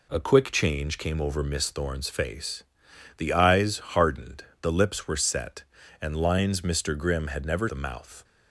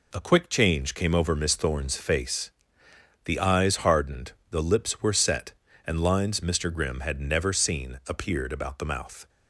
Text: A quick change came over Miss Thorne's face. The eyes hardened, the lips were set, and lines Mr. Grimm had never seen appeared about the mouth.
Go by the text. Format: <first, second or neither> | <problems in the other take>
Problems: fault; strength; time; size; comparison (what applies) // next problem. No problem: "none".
second | skips "seen appeared about"; at 7.6 s